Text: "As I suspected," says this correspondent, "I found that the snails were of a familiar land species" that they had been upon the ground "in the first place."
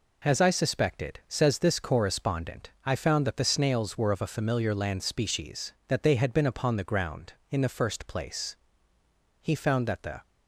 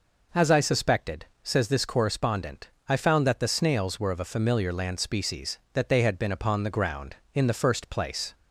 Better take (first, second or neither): second